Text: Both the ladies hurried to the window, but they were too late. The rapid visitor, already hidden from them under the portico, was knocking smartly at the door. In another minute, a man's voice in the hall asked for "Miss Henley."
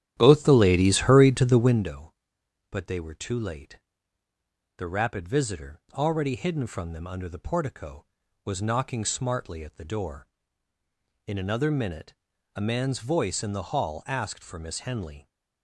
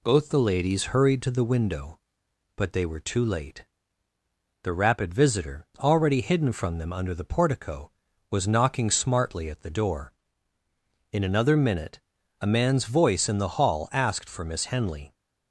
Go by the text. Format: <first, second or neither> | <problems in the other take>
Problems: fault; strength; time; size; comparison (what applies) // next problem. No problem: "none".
second | starts louder than the rest; strong; until 2.0 s; 11 dB